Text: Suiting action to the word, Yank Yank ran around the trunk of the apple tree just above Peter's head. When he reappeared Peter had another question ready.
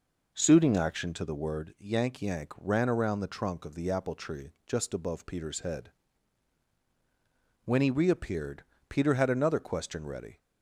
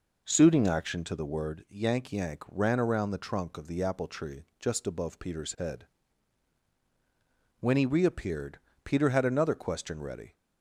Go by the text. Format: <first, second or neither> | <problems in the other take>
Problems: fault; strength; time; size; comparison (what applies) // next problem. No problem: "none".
neither | pauses between "reappeared" and "Peter"; slight; the same in both